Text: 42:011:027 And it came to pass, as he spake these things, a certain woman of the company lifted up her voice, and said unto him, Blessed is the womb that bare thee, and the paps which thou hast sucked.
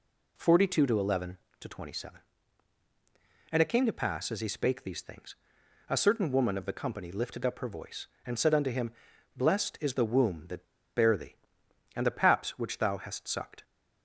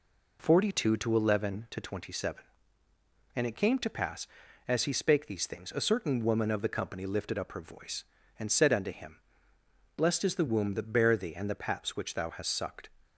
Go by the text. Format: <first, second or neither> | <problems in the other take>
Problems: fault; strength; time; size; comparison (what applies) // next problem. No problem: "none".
second | pauses between "that" and "bare"; slight; at 10.6 s; 0.31 s long